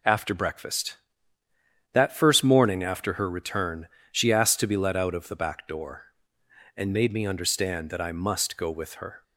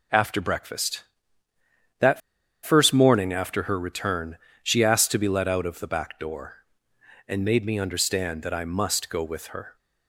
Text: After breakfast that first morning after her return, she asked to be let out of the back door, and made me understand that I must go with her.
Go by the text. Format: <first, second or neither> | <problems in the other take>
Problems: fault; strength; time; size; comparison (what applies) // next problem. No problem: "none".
first | pauses between "that" and "first"; at 2.2 s; 0.45 s long